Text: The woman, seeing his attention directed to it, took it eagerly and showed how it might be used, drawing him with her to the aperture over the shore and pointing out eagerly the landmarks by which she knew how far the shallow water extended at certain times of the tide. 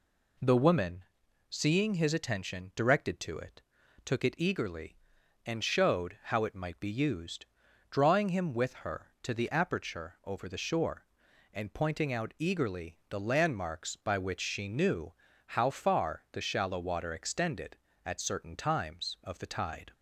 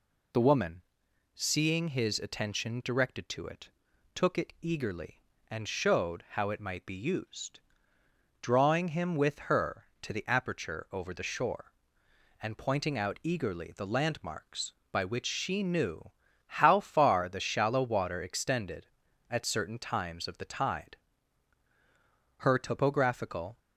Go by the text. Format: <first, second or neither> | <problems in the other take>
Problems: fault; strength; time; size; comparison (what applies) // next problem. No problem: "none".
first | pauses between "knew" and "how"; slight; at 16.0 s; 0.36 s long; slight in the first // goes on to say "Her topographical"; noticeable; from 22.3 s on; 1.2 s long